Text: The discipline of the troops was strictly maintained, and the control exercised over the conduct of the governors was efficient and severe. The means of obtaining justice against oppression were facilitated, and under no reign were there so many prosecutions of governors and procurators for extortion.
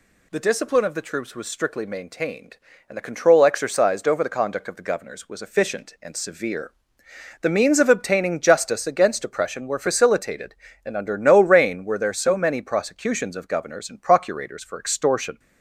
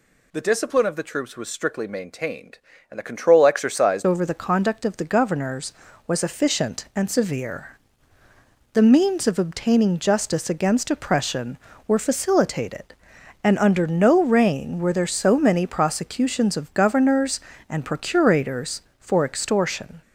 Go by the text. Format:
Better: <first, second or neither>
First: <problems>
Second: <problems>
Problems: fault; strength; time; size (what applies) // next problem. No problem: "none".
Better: first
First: none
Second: changes voice at "over"; from 4.0 s on; 16.0 s long